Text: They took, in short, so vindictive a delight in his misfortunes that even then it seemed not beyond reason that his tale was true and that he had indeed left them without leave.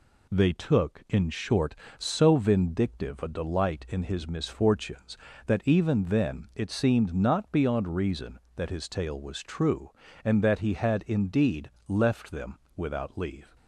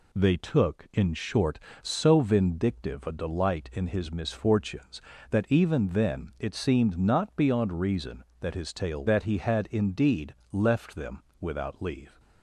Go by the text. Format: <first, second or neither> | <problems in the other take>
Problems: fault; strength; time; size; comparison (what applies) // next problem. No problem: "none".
first | skips "was true and"; at 9.0 s // pauses between "indeed" and "left"; slight; at 10.3 s; 0.16 s long; slight in the first // pauses between "them" and "without"; slight; at 11.2 s; 0.16 s long; slight in the first